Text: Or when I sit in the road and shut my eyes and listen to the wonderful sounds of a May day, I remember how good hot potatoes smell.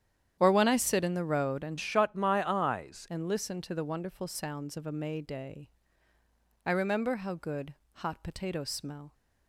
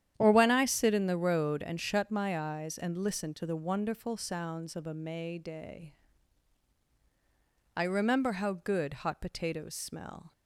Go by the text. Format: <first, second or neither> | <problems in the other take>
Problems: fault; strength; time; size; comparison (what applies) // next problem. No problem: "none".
second | starts louder than the rest; strong; until 1.4 s; 10 dB; strong in the second // changes voice from "shut" to "eyes"; from 1.7 to 3.0 s; 1.3 s long // pauses between "good" and "hot"; slight; at 7.7 s; 0.22 s long